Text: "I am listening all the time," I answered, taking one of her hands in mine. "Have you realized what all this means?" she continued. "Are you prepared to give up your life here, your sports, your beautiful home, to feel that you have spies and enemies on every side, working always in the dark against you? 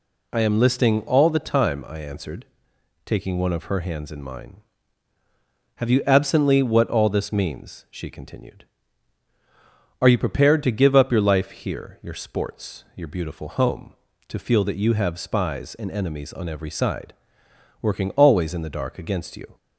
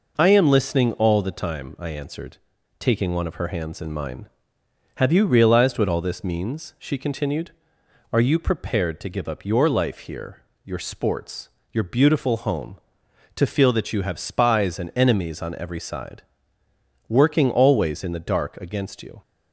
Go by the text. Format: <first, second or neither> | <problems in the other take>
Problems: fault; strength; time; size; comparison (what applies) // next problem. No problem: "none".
second | says "absently" for "realized"; at 6.0 s